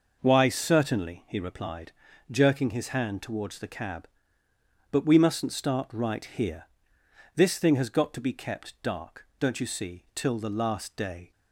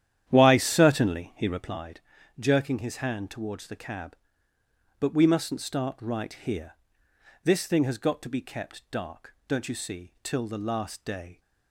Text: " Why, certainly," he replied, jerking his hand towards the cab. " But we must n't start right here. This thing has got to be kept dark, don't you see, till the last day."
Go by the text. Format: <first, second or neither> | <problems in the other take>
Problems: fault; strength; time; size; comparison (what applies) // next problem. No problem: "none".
first | starts louder than the rest; strong; until 1.8 s; 11 dB